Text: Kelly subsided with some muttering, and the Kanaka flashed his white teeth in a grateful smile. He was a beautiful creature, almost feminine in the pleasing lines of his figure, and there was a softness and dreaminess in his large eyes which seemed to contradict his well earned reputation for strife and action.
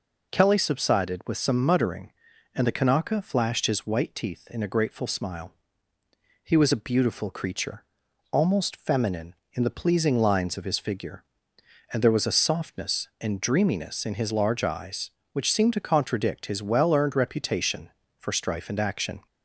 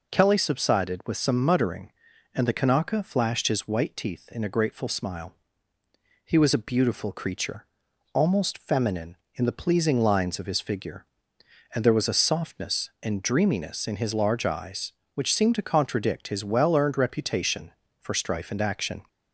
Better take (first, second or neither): neither